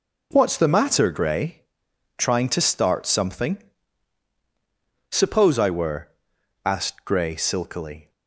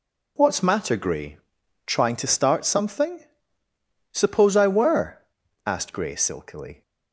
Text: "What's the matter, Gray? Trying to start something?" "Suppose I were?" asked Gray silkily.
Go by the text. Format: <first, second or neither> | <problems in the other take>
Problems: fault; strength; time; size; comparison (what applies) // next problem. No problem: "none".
first | skips "the"; at 0.6 s